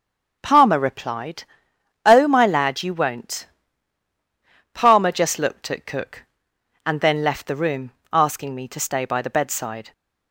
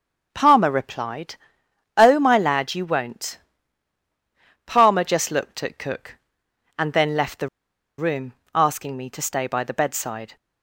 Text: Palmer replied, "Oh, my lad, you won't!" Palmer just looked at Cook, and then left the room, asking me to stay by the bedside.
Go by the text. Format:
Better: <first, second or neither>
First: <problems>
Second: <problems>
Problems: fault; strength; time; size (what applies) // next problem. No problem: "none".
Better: first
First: starts louder than the rest; until 1.4 s; 6.5 dB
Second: starts louder than the rest; until 1.3 s; 6.5 dB // pauses between "the" and "room"; noticeable; at 7.4 s; 0.49 s long